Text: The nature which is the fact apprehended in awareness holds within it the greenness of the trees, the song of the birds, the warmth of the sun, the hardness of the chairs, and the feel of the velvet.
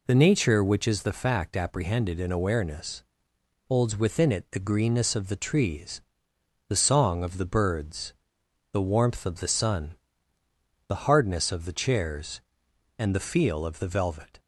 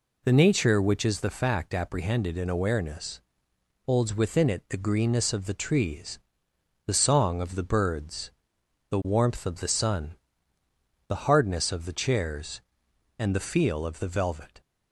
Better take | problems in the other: neither | pauses between "awareness" and "holds"; noticeable; the same in both

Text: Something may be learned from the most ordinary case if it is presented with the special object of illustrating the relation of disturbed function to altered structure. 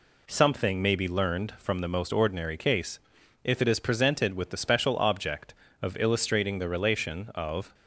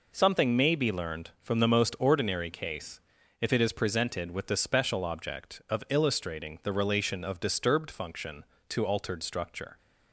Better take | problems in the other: second | pauses between "case" and "if"; at 2.9 s; 0.44 s long; also in the second // stops before "disturbed function to altered structure"; at 7.7 s

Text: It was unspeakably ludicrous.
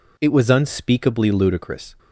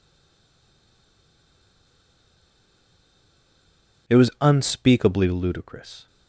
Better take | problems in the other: first | stays silent before the first word; strong; until 4.0 s; 4.0 s long

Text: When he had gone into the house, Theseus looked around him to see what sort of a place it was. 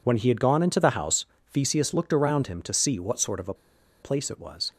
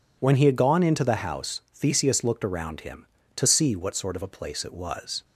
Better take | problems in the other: second | pauses between "a" and "place"; noticeable; at 3.5 s; 0.48 s long

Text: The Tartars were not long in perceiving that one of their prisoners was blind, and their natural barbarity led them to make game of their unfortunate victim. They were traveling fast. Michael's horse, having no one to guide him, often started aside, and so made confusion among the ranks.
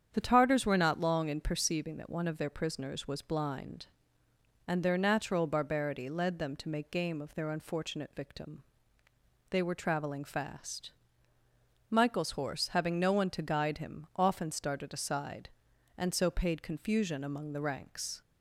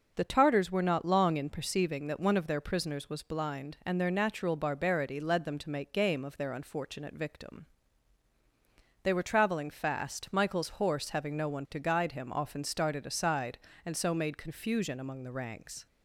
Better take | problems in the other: second | starts louder than the rest; strong; until 1.1 s; 8.5 dB // says "paid" for "made"; at 16.3 s

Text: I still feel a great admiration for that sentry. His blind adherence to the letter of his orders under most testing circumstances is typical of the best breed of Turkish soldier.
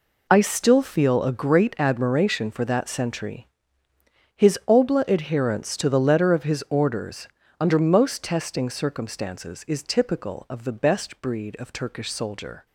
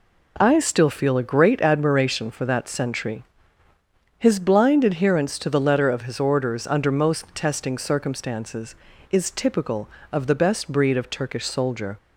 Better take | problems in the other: second | says "obla" for "blind"; at 4.6 s // pauses between "orders" and "under"; slight; at 7.2 s; 0.32 s long

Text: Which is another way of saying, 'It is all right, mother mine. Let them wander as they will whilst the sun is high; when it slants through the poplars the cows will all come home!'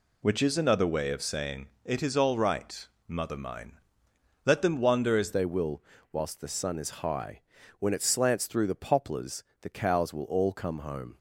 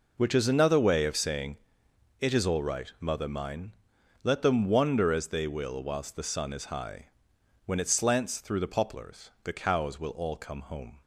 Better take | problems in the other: second | changes voice at "they"; from 5.3 s on; 5.8 s long // pauses between "will" and "whilst"; slight; at 5.8 s; 0.28 s long // pauses between "poplars" and "the"; slight; at 9.4 s; 0.16 s long

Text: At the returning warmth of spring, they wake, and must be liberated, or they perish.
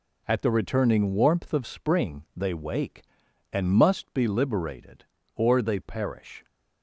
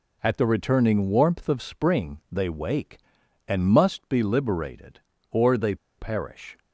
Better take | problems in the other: first | pauses between "they" and "perish"; slight; at 5.7 s; 0.22 s long

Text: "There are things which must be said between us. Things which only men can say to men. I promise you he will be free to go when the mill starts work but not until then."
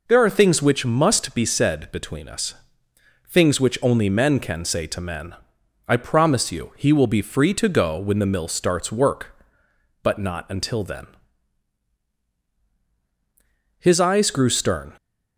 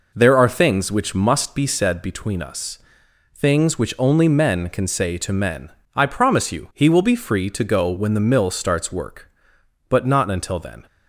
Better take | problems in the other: second | goes on to say "His eyes grew stern"; noticeable; from 13.7 s on; 1.1 s long

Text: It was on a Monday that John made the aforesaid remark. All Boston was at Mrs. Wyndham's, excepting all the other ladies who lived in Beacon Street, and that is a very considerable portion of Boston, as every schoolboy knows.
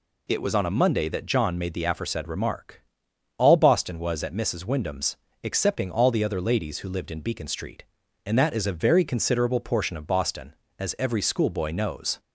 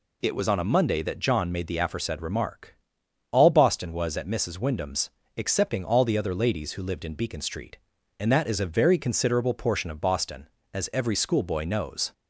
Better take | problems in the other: neither | none

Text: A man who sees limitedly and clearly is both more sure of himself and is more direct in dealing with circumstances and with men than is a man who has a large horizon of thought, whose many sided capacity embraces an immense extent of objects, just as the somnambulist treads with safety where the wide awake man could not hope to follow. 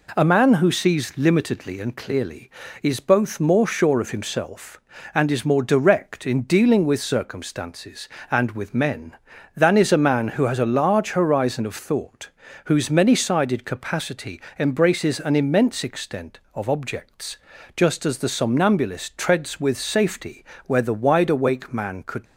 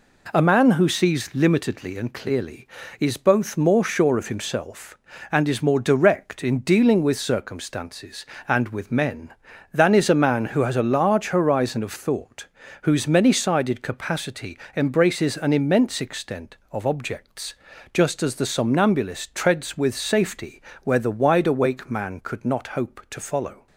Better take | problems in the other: second | pauses between "capacity" and "embraces"; slight; at 14.4 s; 0.16 s long; slight in the second // pauses between "safety" and "where"; slight; at 20.4 s; 0.22 s long; slight in the second // stops before "not hope to follow"; at 22.2 s

